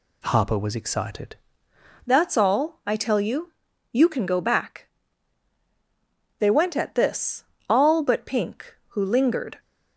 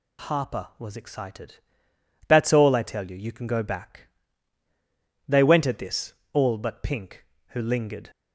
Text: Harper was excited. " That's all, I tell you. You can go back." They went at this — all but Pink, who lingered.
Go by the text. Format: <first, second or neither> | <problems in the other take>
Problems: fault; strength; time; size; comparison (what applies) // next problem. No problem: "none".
second | changes voice at "That's"; from 2.0 s on; 7.5 s long